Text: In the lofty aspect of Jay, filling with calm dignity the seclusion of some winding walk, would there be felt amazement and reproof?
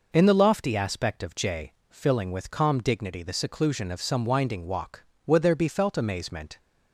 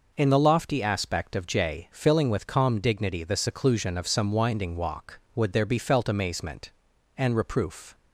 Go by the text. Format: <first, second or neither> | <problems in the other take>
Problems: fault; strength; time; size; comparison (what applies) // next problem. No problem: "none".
second | stops before "and reproof"; at 6.5 s